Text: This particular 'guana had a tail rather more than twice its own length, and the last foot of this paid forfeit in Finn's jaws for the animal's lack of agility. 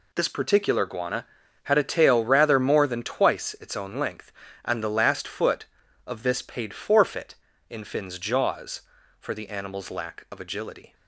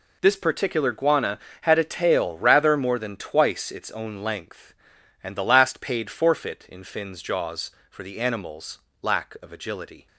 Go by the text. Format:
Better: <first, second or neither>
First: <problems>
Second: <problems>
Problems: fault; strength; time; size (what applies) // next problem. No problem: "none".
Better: first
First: none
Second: skips "foot of this"; at 5.7 s // pauses between "animal's" and "lack"; slight; at 8.7 s; 0.24 s long